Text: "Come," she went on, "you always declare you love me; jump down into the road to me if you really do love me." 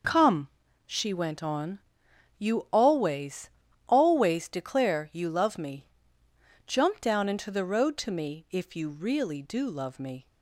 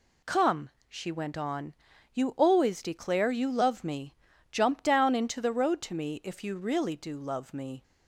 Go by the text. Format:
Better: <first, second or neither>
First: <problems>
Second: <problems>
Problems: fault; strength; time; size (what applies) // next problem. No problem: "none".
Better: second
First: says "always" twice; at 3.8 s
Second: none